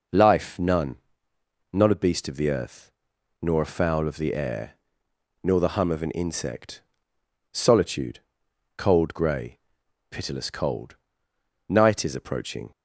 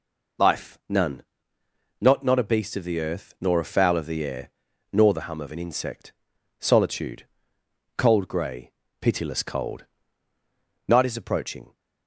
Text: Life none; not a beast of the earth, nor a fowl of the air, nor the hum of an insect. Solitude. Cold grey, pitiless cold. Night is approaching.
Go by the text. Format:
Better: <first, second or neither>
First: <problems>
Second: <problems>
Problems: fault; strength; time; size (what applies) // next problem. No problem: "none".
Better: first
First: none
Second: says "not" twice; at 2.2 s